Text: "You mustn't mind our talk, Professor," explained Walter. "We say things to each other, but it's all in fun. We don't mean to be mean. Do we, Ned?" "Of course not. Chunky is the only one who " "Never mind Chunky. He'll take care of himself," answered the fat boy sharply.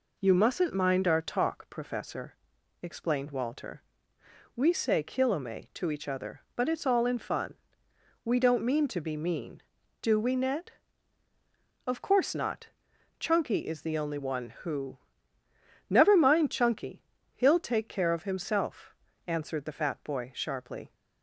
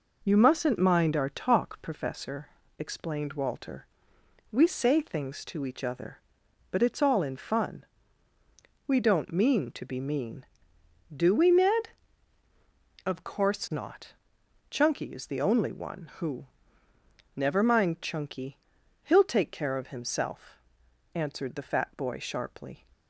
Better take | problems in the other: second | says "kilome" for "things"; at 5.0 s

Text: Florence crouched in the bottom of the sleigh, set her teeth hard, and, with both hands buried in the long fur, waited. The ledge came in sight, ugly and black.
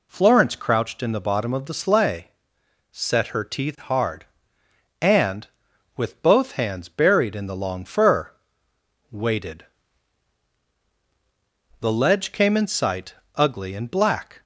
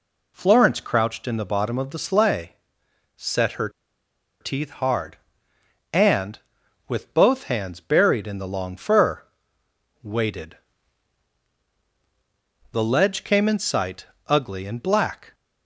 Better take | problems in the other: first | pauses between "her" and "teeth"; noticeable; at 3.6 s; 0.71 s long

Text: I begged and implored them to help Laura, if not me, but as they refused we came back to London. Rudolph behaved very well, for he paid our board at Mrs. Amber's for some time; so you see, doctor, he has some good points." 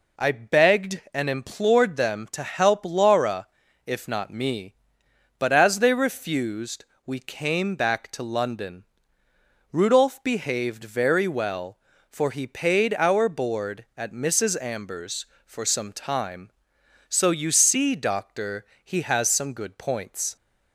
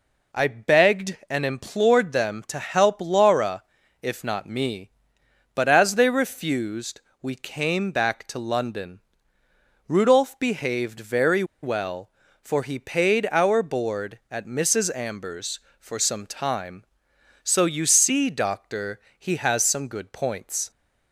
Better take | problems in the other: first | pauses between "refused" and "we"; slight; at 6.9 s; 0.22 s long; slight in the first // pauses between "very" and "well"; slight; at 11.4 s; 0.18 s long

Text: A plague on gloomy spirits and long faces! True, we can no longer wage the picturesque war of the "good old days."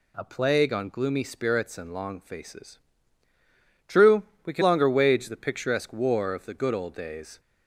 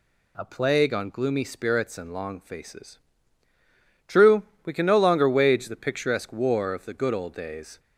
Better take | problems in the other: second | skips "no"; at 4.6 s

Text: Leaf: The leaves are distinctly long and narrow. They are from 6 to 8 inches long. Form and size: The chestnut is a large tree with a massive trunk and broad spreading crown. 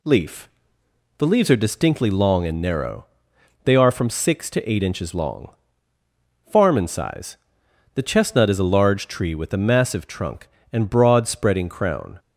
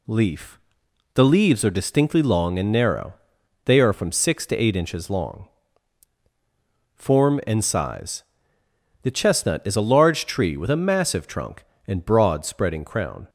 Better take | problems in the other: second | says "Farm" for "Form"; at 6.5 s

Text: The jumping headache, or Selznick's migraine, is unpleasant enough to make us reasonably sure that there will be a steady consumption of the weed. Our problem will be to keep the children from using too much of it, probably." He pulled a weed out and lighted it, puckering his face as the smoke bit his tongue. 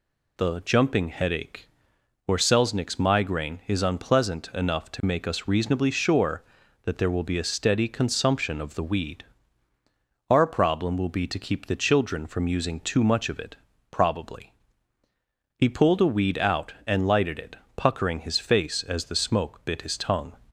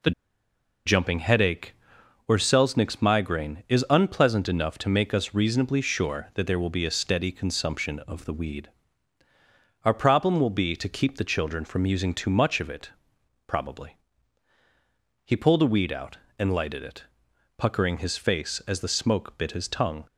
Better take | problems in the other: first | pauses between "The" and "jumping"; noticeable; at 0.1 s; 0.75 s long

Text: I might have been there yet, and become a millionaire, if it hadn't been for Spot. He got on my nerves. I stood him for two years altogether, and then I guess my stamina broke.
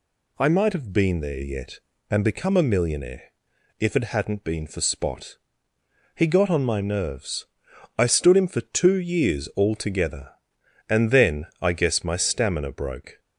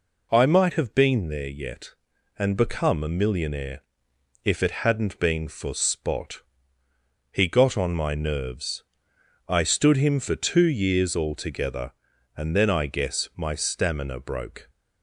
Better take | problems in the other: neither | none

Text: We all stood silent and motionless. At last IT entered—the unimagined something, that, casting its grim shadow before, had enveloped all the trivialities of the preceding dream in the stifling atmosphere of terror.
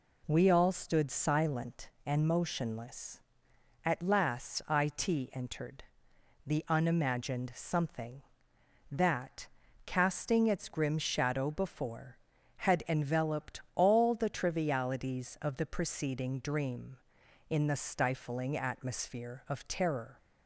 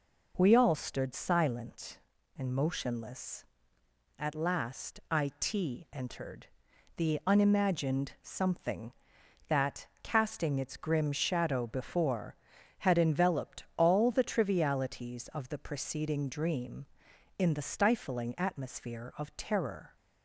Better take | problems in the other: neither | none

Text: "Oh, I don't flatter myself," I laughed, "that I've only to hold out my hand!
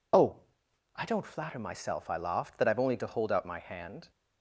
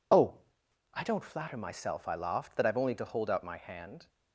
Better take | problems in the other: first | gets quieter; strong; throughout; 8 dB

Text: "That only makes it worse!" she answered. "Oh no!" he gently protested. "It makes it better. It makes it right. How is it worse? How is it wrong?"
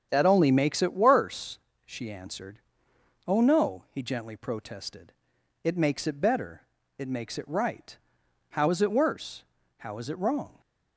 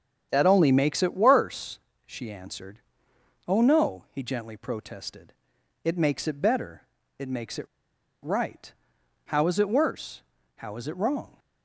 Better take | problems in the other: first | starts louder than the rest; strong; until 1.3 s; 8 dB; strong in the first // pauses between "it" and "right"; noticeable; at 7.6 s; 0.55 s long

